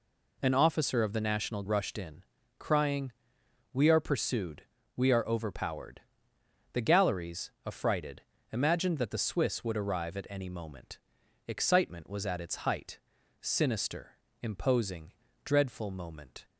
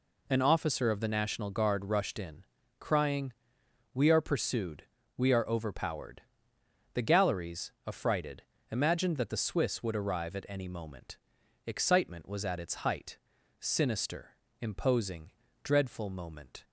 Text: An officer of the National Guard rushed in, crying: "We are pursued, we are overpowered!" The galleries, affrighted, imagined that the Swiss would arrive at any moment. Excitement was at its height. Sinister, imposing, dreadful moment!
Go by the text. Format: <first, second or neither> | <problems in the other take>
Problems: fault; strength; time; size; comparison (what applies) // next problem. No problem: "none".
second | skips "Guard"; at 1.6 s